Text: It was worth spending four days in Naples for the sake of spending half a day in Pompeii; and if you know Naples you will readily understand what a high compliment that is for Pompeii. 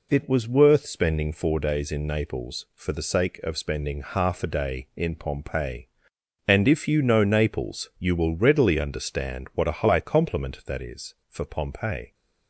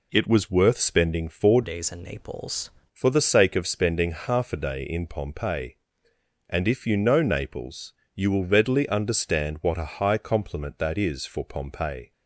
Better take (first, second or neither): first